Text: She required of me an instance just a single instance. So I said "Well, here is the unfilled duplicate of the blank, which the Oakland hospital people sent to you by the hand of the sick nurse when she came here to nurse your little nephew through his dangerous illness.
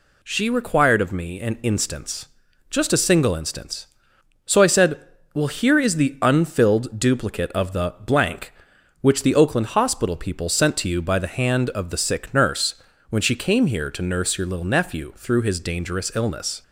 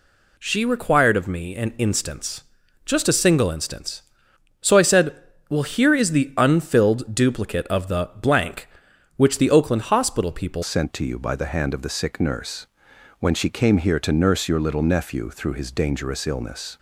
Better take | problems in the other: first | pauses between "instance" and "just"; at 2.4 s; 0.42 s long; also in the first // pauses between "said" and "Well"; slight; at 5.1 s; 0.36 s long; slight in the first // changes voice at "sent"; from 10.6 s on; 6.1 s long // pauses between "nurse" and "when"; noticeable; at 12.6 s; 0.54 s long; slight in the first

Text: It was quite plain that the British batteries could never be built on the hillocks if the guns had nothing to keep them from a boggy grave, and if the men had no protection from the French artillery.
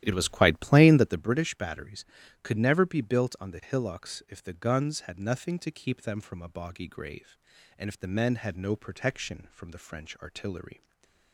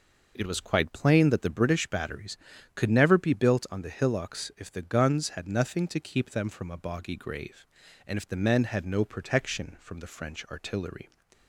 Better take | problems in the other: second | starts louder than the rest; strong; until 1.2 s; 13 dB // stays silent after the last word; slight; from 10.7 s on; 0.6 s long

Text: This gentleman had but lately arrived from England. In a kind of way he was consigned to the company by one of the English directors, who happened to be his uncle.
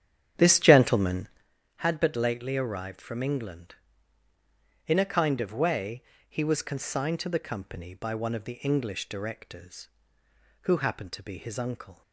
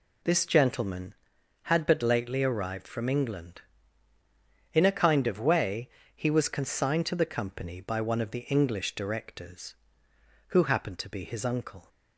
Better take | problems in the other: second | starts louder than the rest; strong; until 1.5 s; 9.5 dB // pauses between "way" and "he"; slight; at 6.0 s; 0.26 s long; slight in the second

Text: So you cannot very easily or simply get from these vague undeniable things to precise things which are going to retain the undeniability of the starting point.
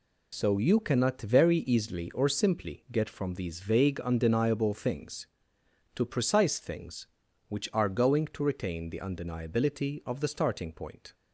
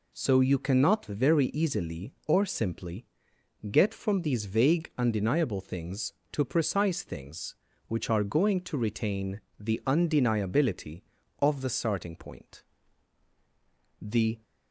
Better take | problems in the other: first | pauses between "simply" and "get"; noticeable; at 3.0 s; 0.66 s long // pauses between "retain" and "the"; slight; at 9.3 s; 0.18 s long // goes on to say "The"; slight; from 13.9 s on; 0.44 s long

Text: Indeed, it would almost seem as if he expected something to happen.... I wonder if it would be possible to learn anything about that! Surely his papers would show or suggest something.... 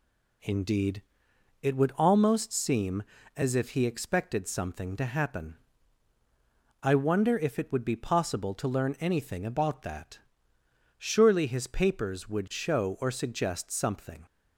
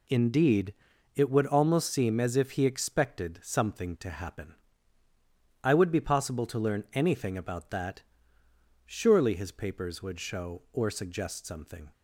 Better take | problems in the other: first | skips "wonder if it"; at 5.7 s

